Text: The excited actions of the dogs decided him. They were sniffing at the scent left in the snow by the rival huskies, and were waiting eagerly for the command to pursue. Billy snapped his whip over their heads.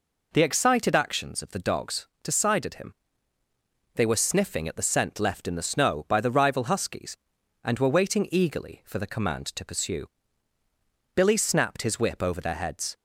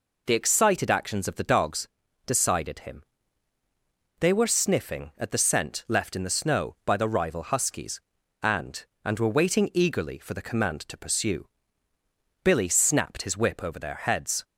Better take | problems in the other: first | pauses between "dogs" and "decided"; at 1.8 s; 0.38 s long; slight in the first // says "and" twice; at 9.0 s

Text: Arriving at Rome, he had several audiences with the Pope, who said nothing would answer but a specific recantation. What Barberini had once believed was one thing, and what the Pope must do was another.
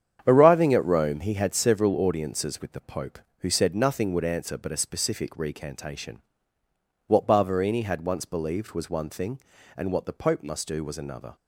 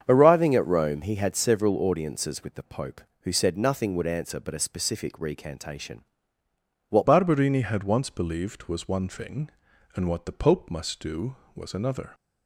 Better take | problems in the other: first | starts louder than the rest; strong; until 1.0 s; 7.5 dB; strong in the first // changes voice at "Barberini"; from 7.0 s on; 5.1 s long

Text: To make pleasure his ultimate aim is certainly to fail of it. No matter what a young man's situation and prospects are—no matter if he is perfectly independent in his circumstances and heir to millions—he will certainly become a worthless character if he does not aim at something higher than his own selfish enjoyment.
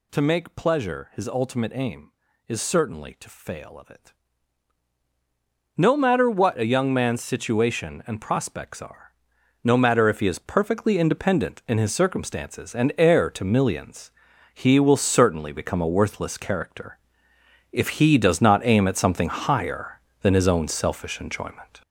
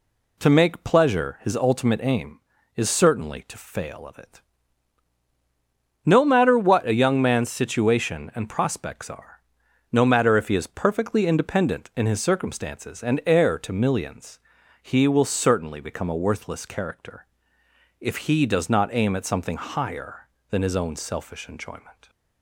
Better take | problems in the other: second | gets louder; noticeable; throughout; 5.5 dB // pauses between "character" and "if"; noticeable; at 16.9 s; 0.74 s long; noticeable in the second

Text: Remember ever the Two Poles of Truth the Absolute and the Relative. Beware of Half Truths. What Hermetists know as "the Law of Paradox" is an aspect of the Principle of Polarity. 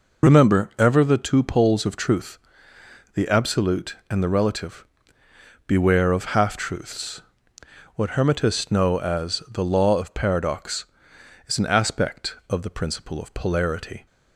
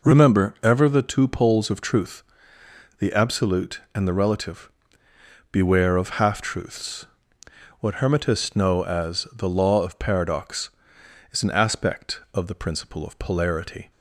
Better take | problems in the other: second | loses the start of "Remember"; at 0.2 s; 35 ms // pauses between "Truth" and "the"; noticeable; at 2.3 s; 0.74 s long; noticeable in the second

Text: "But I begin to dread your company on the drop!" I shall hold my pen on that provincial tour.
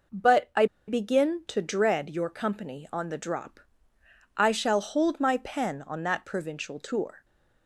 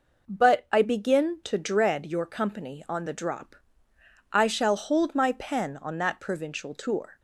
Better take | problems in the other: second | pauses between "I" and "begin"; slight; at 0.6 s; 0.22 s long

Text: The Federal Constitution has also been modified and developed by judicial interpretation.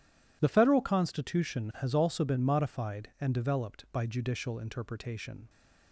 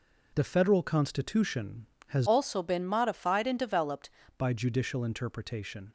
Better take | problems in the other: first | changes voice from "also" to "developed"; from 2.2 to 4.0 s; 1.8 s long

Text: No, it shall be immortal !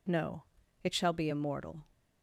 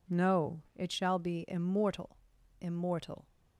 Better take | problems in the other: first | says "immortal" twice; at 2.5 s

